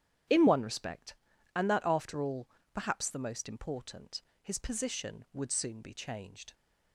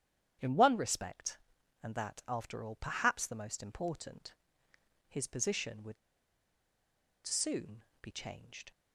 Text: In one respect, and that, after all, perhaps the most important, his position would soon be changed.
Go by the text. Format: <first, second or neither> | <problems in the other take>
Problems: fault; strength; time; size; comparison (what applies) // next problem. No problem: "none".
first | starts louder than the rest; strong; until 1.8 s; 9.5 dB; strong in the first // pauses between "would" and "soon"; strong; at 5.9 s; 1.3 s long // pauses between "soon" and "be"; slight; at 7.8 s; 0.18 s long